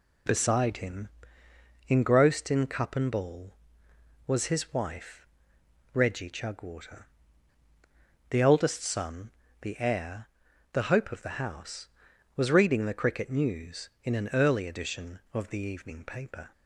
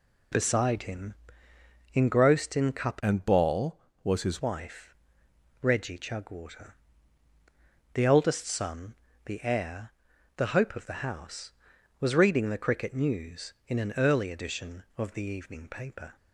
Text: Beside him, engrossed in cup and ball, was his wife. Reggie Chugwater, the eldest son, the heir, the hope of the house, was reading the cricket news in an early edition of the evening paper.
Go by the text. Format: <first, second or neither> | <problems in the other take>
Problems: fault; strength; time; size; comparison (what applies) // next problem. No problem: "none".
first | changes voice from "and" to "his"; from 3.0 to 4.4 s; 1.4 s long